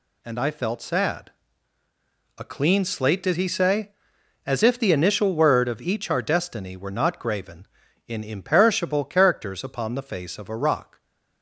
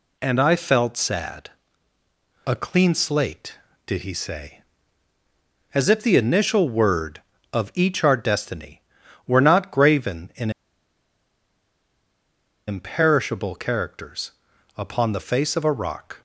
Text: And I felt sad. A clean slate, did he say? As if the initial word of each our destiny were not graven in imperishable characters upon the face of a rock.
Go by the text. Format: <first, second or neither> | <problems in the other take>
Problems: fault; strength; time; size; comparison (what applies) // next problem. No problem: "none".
first | pauses between "in" and "imperishable"; strong; at 10.5 s; 2.1 s long // pauses between "characters" and "upon"; noticeable; at 14.3 s; 0.46 s long